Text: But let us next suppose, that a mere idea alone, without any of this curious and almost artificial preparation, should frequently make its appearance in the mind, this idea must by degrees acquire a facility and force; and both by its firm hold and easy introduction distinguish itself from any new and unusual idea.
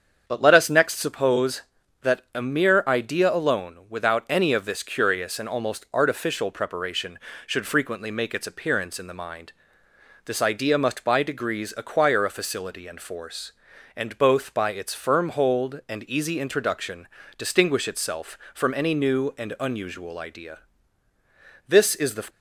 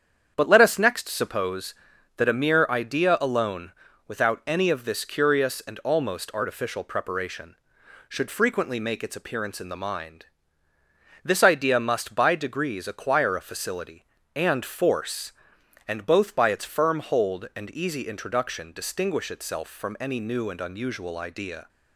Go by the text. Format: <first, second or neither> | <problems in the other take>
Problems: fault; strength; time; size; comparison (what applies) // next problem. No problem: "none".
second | starts louder than the rest; strong; until 1.2 s; 7.5 dB; strong in the second // pauses between "introduction" and "distinguish"; slight; at 17.0 s; 0.32 s long // goes on to say "This is the"; from 21.6 s on; 0.60 s long